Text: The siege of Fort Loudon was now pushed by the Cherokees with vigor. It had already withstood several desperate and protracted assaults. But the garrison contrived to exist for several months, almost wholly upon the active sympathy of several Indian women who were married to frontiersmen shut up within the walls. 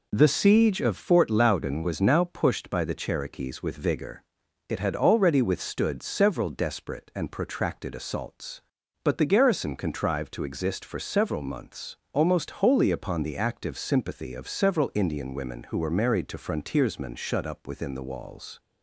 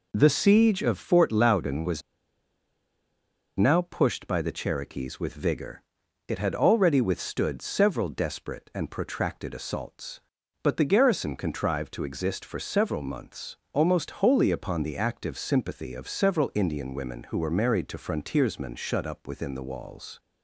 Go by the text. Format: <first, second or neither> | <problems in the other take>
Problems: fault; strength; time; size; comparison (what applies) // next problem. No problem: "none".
first | pauses between "was" and "now"; strong; at 2.0 s; 1.5 s long